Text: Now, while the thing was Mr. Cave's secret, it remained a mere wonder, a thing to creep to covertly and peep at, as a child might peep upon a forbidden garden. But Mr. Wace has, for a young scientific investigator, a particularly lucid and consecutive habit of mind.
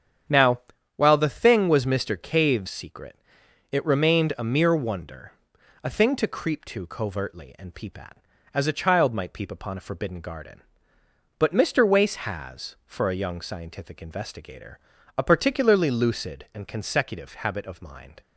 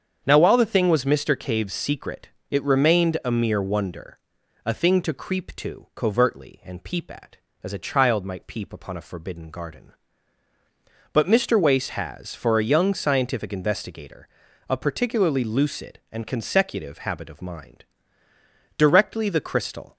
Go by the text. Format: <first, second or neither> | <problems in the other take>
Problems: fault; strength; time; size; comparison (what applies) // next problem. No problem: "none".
first | starts louder than the rest; strong; until 1.2 s; 7.5 dB; strong in the first // goes on to say "Directly the crystal"; noticeable; from 18.7 s on; 1.1 s long